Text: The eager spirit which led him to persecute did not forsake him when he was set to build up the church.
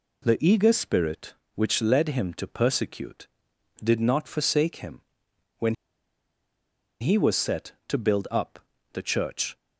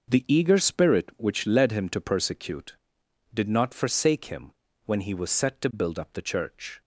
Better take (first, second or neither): second